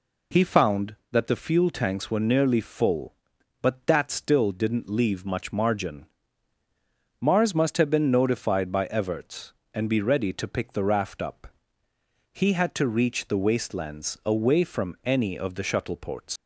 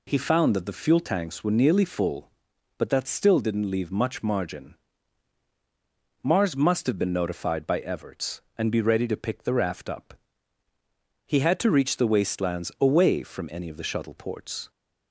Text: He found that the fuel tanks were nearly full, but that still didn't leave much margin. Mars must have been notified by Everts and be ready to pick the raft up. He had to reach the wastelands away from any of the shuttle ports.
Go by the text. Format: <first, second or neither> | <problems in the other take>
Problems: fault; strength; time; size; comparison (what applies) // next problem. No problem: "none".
second | leaves "ports" unfinished; at 16.3 s; 120 ms